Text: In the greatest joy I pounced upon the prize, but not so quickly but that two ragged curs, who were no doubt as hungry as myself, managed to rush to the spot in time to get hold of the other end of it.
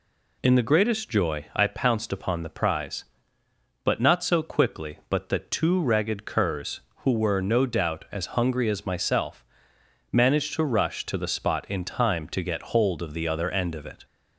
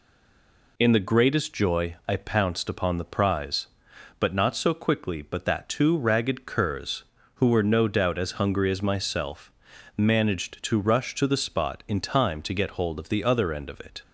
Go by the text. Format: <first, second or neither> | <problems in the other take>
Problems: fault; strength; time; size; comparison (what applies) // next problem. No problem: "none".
first | stays silent before the first word; slight; until 0.7 s; 0.7 s long